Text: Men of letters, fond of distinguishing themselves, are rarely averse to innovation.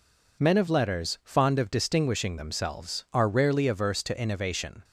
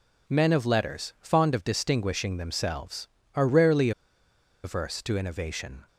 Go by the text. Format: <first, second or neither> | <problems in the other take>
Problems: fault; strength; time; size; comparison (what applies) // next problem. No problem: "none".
first | pauses between "rarely" and "averse"; noticeable; at 3.9 s; 0.73 s long